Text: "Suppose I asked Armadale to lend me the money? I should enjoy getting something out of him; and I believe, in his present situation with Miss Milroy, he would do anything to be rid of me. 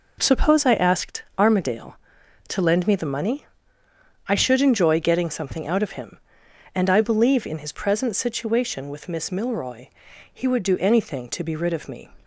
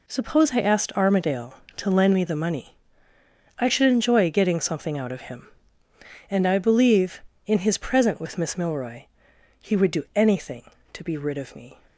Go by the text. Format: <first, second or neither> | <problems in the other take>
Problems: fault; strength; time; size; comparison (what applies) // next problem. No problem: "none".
first | skips "situation"; at 8.1 s